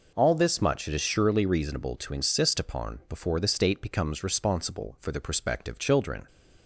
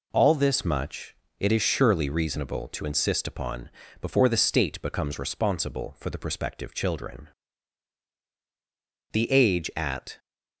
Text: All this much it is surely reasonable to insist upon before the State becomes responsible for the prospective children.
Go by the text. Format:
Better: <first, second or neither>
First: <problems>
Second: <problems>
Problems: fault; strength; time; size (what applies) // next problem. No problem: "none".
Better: first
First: none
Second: pauses between "much" and "it"; slight; at 1.1 s; 0.24 s long // pauses between "upon" and "before"; slight; at 3.6 s; 0.32 s long // goes on to say "The age at"; noticeable; from 9.1 s on; 1.0 s long